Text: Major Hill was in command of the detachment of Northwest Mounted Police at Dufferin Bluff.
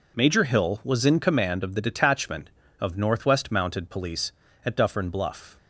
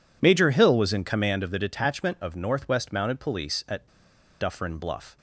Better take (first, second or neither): first